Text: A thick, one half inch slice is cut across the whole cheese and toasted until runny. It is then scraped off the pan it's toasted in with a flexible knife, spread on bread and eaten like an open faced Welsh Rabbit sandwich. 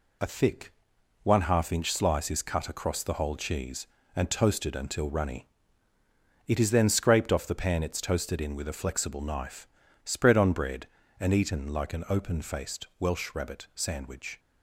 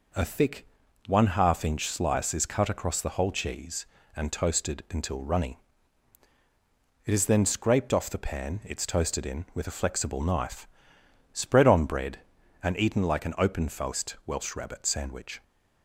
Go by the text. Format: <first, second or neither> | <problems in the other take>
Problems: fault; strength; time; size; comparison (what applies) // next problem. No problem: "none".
neither | none